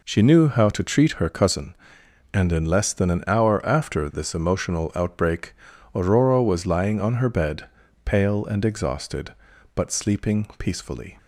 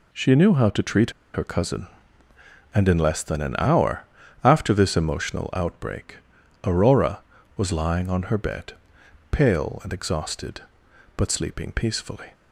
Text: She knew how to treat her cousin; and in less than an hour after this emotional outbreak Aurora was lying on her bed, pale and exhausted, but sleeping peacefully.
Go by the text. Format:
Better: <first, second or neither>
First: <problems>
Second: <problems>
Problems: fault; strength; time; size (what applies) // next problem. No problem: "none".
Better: first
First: pauses between "outbreak" and "Aurora"; at 5.5 s; 0.42 s long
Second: pauses between "treat" and "her"; slight; at 1.1 s; 0.22 s long // pauses between "hour" and "after"; at 4.0 s; 0.40 s long // pauses between "outbreak" and "Aurora"; noticeable; at 6.1 s; 0.48 s long